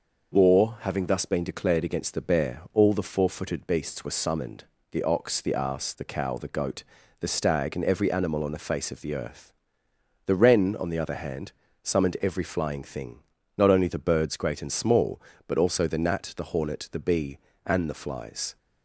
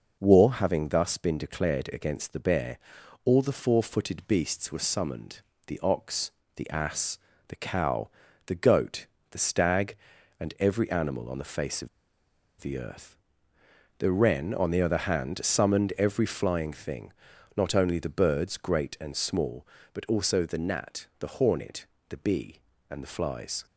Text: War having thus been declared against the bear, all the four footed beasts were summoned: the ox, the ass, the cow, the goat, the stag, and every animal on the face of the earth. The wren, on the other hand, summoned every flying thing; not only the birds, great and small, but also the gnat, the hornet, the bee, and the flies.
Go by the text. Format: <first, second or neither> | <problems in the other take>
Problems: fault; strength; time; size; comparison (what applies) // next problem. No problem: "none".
first | pauses between "of" and "the"; noticeable; at 11.8 s; 0.72 s long